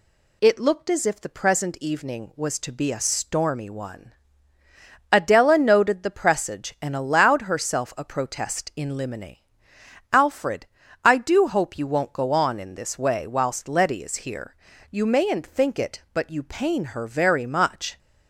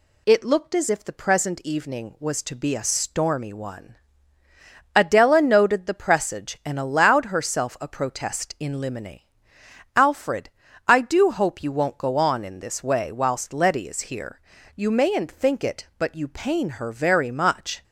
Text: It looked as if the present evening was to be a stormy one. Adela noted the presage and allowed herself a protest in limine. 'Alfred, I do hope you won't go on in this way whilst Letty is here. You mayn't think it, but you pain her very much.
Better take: neither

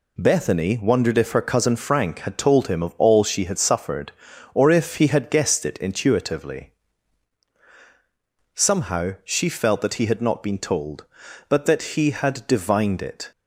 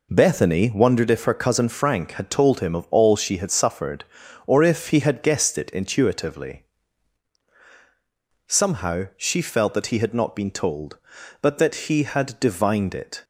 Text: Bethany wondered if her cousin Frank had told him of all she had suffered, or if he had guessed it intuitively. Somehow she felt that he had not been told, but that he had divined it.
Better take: first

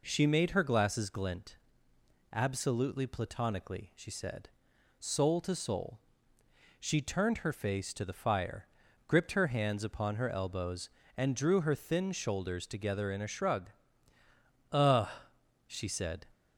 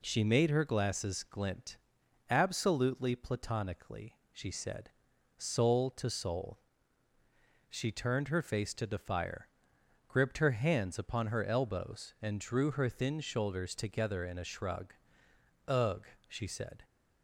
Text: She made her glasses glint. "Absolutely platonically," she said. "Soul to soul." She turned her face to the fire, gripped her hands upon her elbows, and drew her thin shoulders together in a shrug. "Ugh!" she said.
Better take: neither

